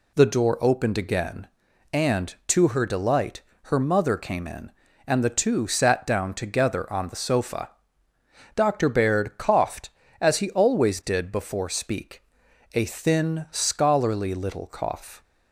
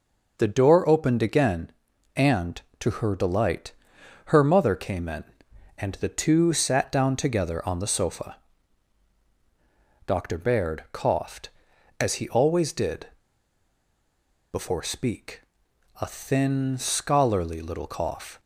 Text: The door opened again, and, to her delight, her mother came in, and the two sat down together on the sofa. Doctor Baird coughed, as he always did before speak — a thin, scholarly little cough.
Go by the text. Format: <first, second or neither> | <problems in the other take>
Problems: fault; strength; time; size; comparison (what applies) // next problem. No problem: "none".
first | pauses between "did" and "before"; strong; at 13.0 s; 1.4 s long